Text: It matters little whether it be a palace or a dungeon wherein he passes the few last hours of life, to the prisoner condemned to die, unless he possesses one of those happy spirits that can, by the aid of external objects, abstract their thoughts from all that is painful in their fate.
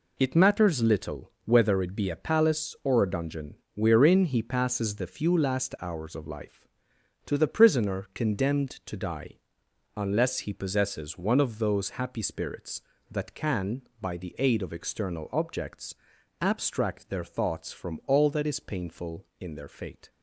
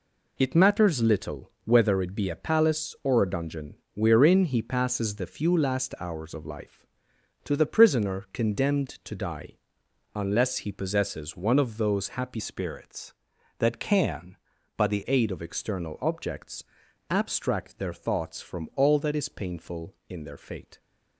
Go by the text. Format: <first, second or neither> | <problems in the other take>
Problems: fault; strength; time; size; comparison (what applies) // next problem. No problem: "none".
first | pauses between "dungeon" and "wherein"; slight; at 3.7 s; 0.18 s long; slight in the first // changes voice from "spirits" to "the"; from 12.3 to 15.0 s; 2.7 s long